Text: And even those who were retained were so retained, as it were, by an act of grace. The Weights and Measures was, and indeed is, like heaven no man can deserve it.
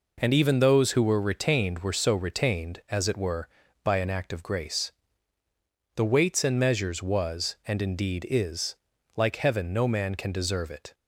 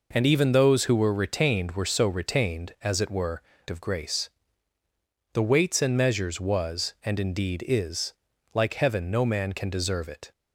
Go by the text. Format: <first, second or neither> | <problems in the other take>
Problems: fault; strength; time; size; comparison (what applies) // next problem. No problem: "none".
first | skips "by an act"; at 3.5 s